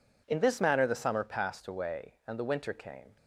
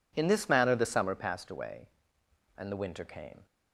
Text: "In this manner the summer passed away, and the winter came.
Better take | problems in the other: neither | none

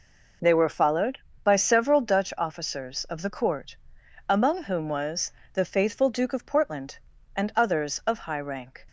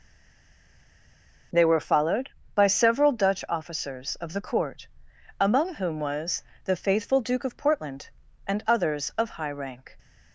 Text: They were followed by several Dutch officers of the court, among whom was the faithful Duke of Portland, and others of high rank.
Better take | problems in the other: first | stays silent before the first word; noticeable; until 1.5 s; 1.5 s long // pauses between "was" and "the"; slight; at 6.4 s; 0.20 s long; slight in the first

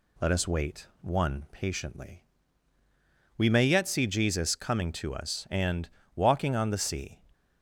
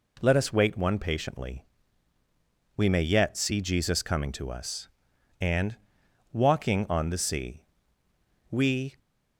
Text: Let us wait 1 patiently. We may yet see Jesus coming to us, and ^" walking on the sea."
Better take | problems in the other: first | goes on to say "We"; slight; from 8.4 s on; 0.48 s long

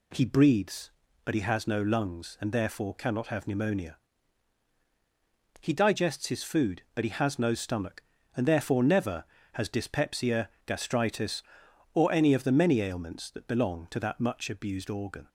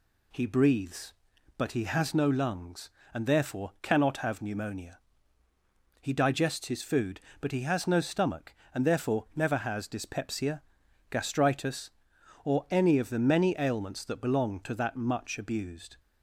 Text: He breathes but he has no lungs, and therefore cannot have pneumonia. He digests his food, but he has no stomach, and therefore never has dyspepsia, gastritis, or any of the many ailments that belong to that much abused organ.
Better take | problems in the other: first | stops before "organ"; at 15.9 s

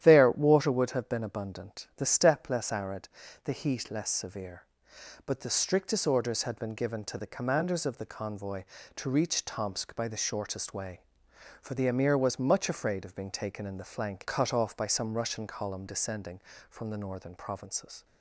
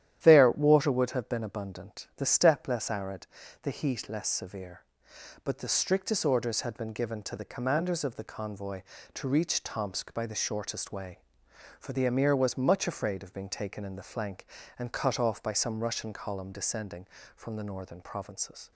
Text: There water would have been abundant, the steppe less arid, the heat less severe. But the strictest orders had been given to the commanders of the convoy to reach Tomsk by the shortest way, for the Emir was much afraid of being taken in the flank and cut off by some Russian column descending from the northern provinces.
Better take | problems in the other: second | starts louder than the rest; strong; until 1.0 s; 11 dB; strong in the second // skips "and"; at 14.2 s

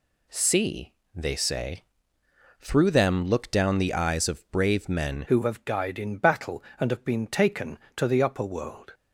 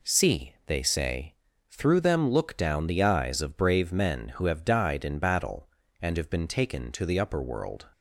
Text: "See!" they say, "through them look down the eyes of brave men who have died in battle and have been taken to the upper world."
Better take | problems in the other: second | changes voice at "who"; from 5.2 s on; 3.7 s long

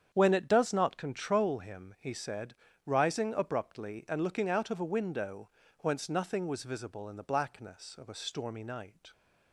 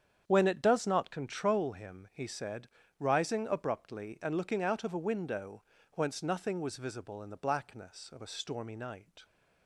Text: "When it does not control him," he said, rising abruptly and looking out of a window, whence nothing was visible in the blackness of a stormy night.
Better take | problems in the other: neither | starts louder than the rest; strong; the same in both

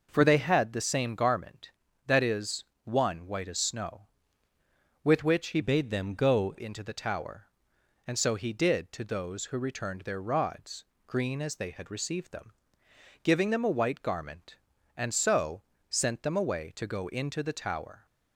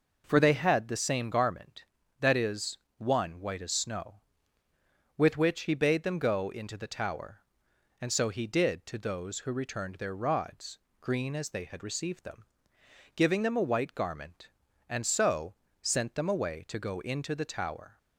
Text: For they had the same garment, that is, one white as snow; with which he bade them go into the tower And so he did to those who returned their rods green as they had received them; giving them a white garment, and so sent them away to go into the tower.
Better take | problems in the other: second | changes voice from "bade" to "go"; from 5.6 to 6.5 s; 0.9 s long // pauses between "rods" and "green"; slight; at 10.8 s; 0.22 s long; slight in the second // pauses between "so" and "sent"; slight; at 15.6 s; 0.26 s long; slight in the second

